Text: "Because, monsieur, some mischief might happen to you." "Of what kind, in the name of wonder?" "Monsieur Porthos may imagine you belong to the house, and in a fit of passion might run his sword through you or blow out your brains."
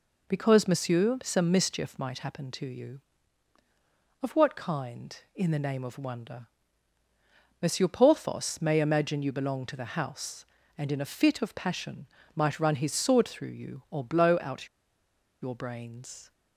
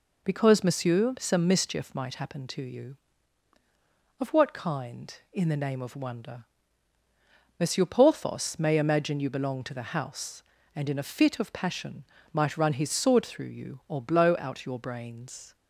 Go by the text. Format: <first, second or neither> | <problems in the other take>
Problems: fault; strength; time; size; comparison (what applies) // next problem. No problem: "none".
second | pauses between "passion" and "might"; slight; at 12.0 s; 0.28 s long; slight in the second // pauses between "out" and "your"; noticeable; at 14.6 s; 0.73 s long